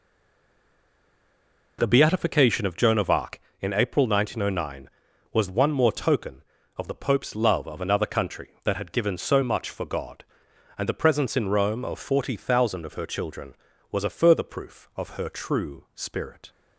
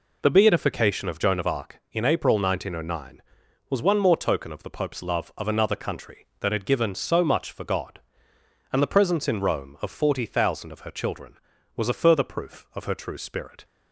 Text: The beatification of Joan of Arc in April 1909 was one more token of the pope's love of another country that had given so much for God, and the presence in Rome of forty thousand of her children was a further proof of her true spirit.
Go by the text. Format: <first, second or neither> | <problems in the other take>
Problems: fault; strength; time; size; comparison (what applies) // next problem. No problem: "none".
second | stays silent before the first word; noticeable; until 1.7 s; 1.7 s long